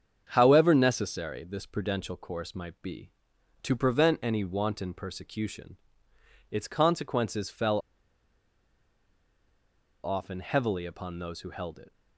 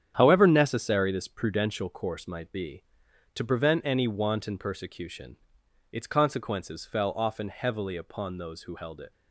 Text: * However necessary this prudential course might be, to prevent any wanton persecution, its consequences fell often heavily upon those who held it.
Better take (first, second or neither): second